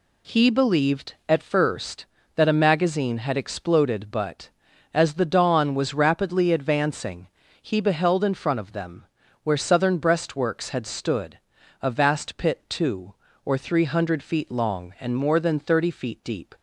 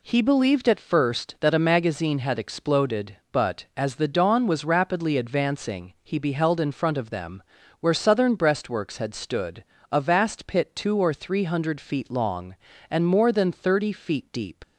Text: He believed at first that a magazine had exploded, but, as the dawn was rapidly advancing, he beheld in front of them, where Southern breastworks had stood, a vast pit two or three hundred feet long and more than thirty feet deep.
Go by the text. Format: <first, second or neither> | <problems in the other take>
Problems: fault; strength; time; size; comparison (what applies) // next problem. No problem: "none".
first | leaves "deep" unfinished; at 14.6 s; 70 ms